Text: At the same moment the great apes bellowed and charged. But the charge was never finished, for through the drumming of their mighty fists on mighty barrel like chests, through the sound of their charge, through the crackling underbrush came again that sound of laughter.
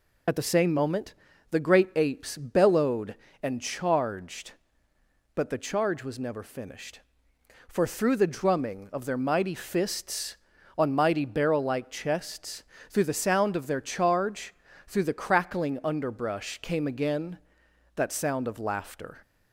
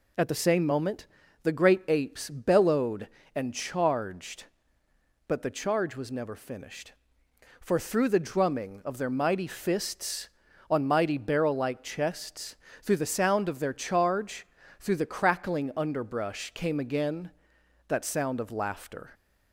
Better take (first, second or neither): second